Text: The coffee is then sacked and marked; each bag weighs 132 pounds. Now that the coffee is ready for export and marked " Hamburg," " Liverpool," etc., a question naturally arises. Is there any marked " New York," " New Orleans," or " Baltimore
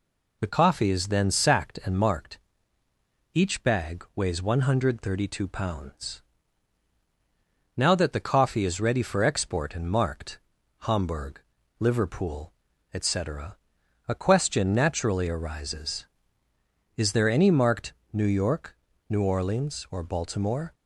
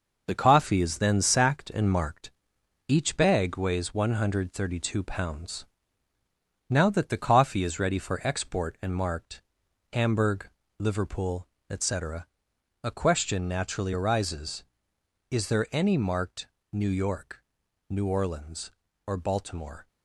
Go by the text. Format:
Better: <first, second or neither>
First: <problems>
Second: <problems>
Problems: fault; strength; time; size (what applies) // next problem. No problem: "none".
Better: first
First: none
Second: gets quieter; strong; throughout; 10.5 dB